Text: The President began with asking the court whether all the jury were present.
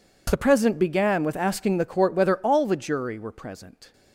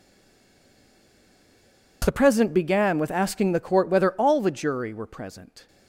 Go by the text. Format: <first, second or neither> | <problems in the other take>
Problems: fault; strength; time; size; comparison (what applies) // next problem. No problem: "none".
first | stays silent before the first word; noticeable; until 2.0 s; 2.0 s long